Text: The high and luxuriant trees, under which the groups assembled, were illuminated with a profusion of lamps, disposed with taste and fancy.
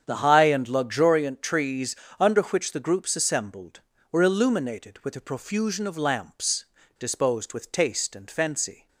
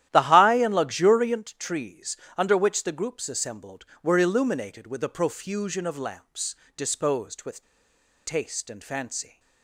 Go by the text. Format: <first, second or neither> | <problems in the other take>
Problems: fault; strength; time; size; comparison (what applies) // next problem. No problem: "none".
first | starts louder than the rest; strong; until 1.1 s; 12 dB; strong in the first // pauses between "with" and "taste"; noticeable; at 7.6 s; 0.65 s long